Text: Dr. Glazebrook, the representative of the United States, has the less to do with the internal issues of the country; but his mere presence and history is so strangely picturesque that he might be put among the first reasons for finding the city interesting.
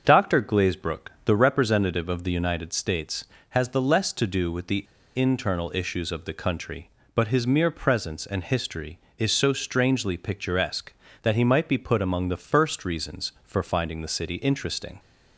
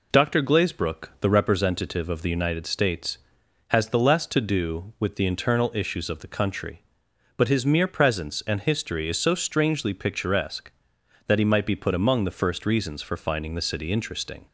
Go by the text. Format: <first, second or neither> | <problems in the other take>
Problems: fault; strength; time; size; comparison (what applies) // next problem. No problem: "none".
second | starts louder than the rest; until 1.0 s; 7 dB // pauses between "the" and "internal"; slight; at 4.8 s; 0.31 s long